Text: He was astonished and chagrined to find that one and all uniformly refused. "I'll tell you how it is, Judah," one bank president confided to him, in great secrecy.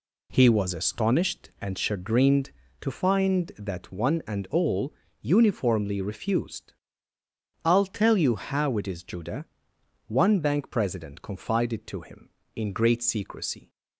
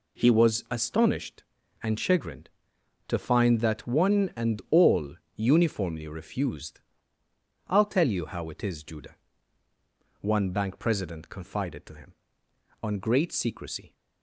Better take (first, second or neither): first